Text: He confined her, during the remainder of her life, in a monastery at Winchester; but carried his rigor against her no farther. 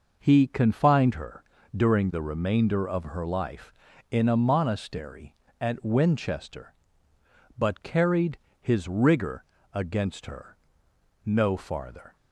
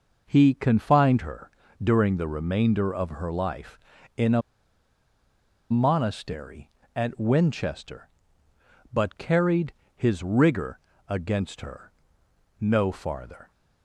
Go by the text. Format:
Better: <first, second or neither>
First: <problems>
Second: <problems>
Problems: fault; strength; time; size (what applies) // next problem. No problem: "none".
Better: first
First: pauses between "carried" and "his"; slight; at 8.3 s; 0.22 s long // pauses between "rigor" and "against"; slight; at 9.4 s; 0.28 s long // pauses between "her" and "no"; noticeable; at 10.5 s; 0.68 s long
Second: pauses between "a" and "monastery"; strong; at 4.4 s; 1.2 s long // pauses between "carried" and "his"; slight; at 9.7 s; 0.22 s long // pauses between "rigor" and "against"; slight; at 10.7 s; 0.28 s long // pauses between "her" and "no"; noticeable; at 11.9 s; 0.68 s long